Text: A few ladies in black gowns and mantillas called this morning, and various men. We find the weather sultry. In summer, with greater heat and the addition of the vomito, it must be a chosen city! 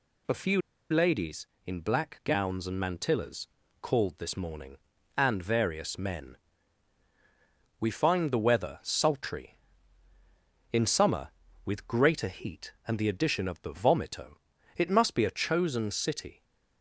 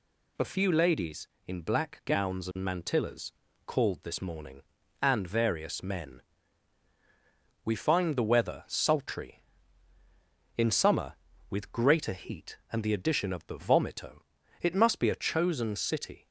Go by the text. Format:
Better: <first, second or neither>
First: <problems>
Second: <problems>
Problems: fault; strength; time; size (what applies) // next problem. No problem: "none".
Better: second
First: pauses between "few" and "ladies"; slight; at 0.5 s; 0.31 s long // pauses between "mantillas" and "called"; slight; at 3.4 s; 0.32 s long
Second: pauses between "mantillas" and "called"; slight; at 3.3 s; 0.32 s long